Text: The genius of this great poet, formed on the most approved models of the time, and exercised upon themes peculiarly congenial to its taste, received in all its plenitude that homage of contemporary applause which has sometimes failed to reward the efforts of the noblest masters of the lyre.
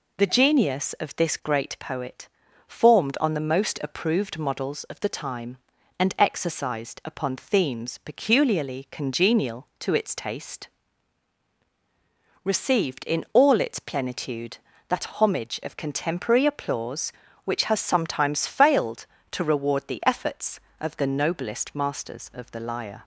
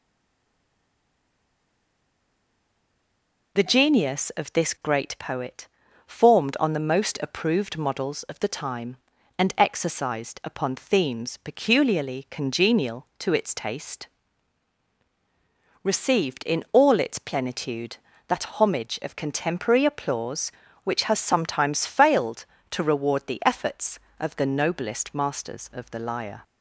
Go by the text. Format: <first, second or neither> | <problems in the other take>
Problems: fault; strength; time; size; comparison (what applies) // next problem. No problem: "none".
first | stays silent before the first word; strong; until 3.5 s; 3.5 s long